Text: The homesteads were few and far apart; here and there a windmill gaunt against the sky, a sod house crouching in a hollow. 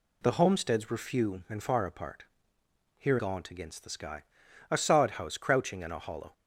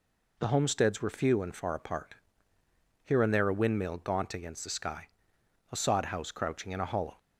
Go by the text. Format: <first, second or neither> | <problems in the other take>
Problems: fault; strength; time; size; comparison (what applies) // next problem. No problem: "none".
second | skips "and there a windmill"; at 3.1 s